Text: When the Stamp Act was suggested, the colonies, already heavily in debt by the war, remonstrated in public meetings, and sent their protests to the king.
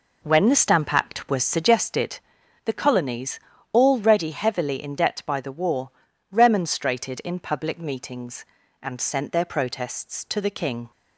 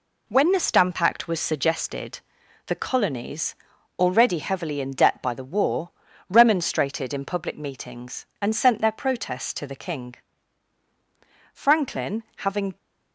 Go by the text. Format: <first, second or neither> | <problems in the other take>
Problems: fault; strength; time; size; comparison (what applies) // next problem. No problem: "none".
first | goes on to say "Franklin having"; noticeable; from 11.5 s on; 1.2 s long